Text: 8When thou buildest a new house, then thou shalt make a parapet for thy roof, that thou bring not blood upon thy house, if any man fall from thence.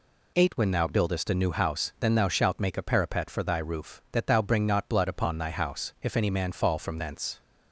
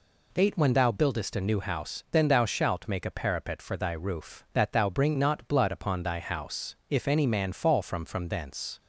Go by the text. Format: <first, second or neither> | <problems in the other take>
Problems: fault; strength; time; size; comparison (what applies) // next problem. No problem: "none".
first | says "from" twice; at 8.0 s